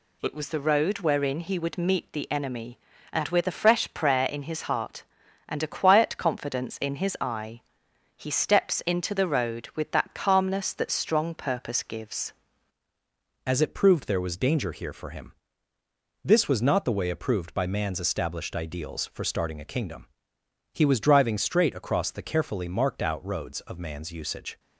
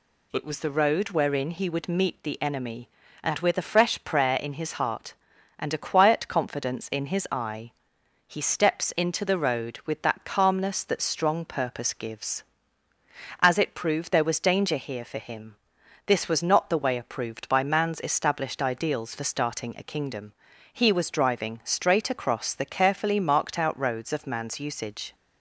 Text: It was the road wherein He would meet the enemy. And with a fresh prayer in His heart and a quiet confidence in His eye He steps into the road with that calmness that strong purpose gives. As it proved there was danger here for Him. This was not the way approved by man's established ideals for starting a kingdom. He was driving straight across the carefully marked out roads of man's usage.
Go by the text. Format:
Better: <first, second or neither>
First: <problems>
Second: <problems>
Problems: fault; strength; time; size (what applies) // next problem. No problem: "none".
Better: second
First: pauses between "eye" and "He"; noticeable; at 7.6 s; 0.56 s long // changes voice at "As"; from 13.4 s on; 11.1 s long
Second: pauses between "eye" and "He"; noticeable; at 7.7 s; 0.56 s long